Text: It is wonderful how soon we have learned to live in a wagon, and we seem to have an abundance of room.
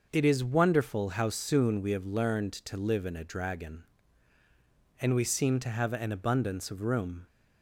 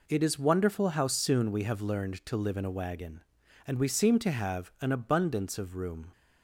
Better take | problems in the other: second | starts louder than the rest; noticeable; until 1.1 s; 6 dB // says "dragon" for "wagon"; at 3.2 s

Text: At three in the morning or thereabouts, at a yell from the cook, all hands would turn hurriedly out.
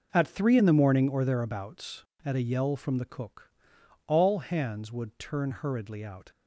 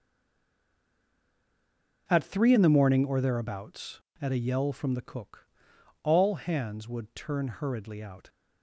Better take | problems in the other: first | stays silent before the first word; noticeable; until 2.0 s; 2.0 s long

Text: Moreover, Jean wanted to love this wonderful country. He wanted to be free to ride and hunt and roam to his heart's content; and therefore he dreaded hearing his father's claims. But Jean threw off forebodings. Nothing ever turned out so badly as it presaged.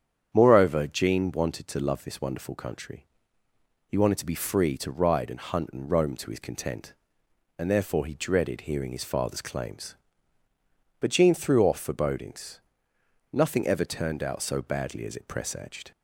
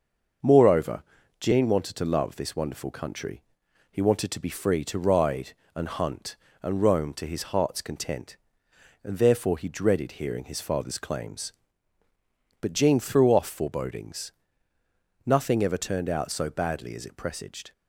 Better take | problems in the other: second | starts louder than the rest; strong; until 1.3 s; 8.5 dB; also in the second // skips "heart's"; at 6.3 s

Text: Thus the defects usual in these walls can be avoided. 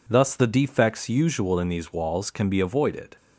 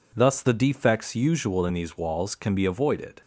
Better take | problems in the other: neither | none

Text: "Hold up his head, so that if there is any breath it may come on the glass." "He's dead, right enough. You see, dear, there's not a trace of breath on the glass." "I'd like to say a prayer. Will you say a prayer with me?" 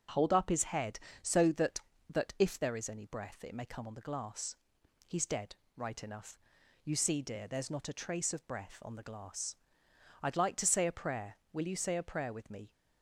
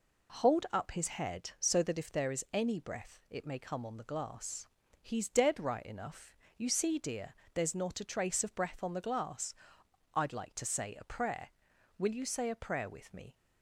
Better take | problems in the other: second | starts louder than the rest; until 1.3 s; 7 dB // says "that" twice; at 2.0 s

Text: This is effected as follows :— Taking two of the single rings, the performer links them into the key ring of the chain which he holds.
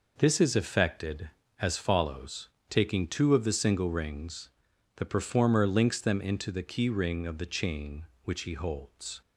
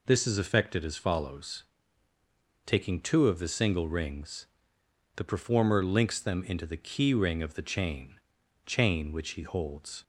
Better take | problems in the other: first | says "chain" twice; at 8.6 s

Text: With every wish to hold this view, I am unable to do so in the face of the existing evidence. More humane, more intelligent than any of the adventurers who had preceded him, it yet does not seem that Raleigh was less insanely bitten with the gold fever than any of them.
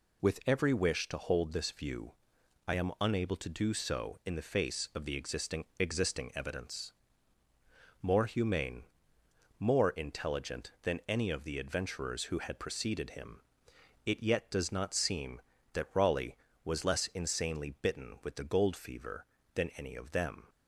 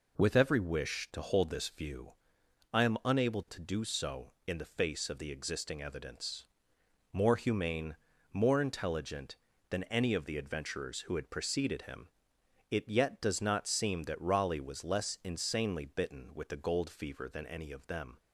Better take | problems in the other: second | says "existing" twice; at 5.7 s

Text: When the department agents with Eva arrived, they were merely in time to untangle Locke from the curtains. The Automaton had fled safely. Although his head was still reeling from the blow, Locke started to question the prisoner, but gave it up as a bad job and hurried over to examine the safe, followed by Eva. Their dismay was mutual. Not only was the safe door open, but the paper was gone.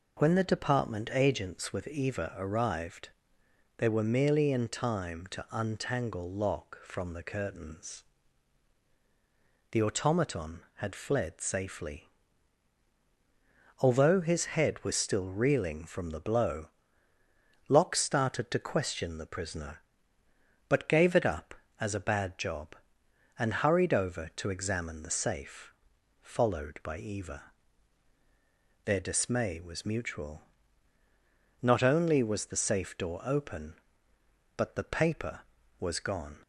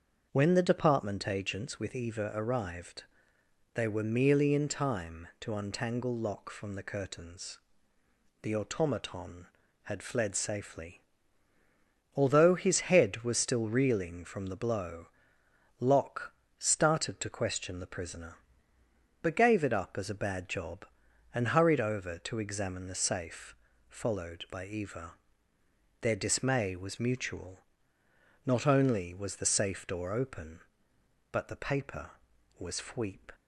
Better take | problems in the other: first | starts louder than the rest; until 1.3 s; 6.5 dB // pauses between "Locke" and "started"; slight; at 16.3 s; 0.28 s long // says "fweep" for "gone"; at 32.7 s

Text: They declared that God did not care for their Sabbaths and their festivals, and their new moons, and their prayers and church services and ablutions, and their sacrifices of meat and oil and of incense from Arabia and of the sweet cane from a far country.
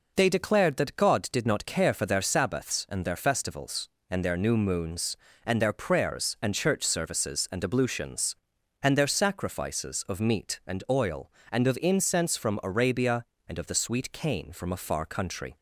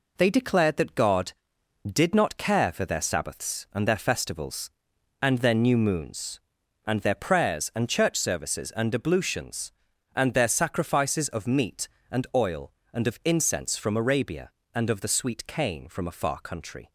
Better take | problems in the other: first | gets quieter; noticeable; throughout; 6 dB

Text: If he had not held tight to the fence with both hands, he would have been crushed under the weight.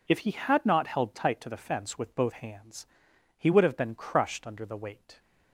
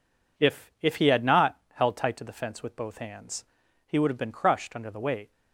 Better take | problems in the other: first | says "If" twice; at 0.8 s

